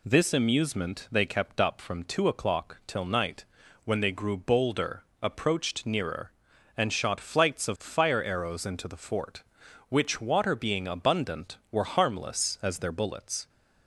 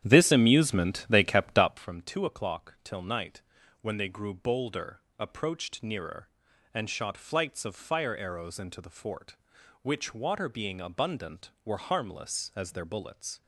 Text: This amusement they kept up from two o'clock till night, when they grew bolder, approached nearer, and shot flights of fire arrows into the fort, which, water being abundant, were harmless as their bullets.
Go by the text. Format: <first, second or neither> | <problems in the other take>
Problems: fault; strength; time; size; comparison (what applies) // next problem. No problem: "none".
first | starts louder than the rest; strong; until 1.9 s; 10.5 dB